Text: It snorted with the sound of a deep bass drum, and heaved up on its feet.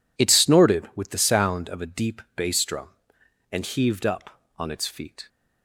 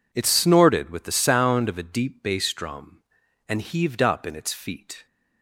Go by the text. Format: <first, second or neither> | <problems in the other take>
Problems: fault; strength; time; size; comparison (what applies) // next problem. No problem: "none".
first | says "in" for "on"; at 4.2 s